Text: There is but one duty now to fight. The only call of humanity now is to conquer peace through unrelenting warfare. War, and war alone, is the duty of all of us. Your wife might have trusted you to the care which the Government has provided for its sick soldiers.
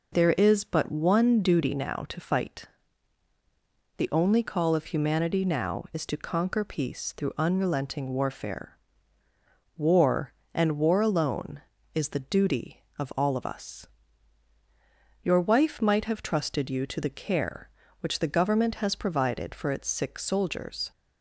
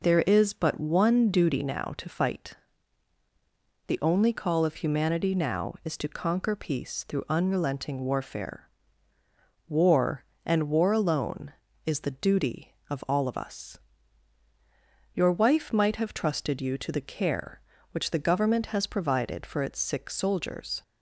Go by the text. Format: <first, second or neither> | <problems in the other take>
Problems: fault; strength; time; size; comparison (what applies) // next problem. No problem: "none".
neither | none